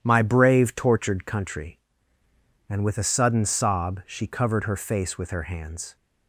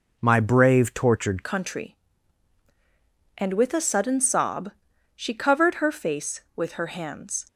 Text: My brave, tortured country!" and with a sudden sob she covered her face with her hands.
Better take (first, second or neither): first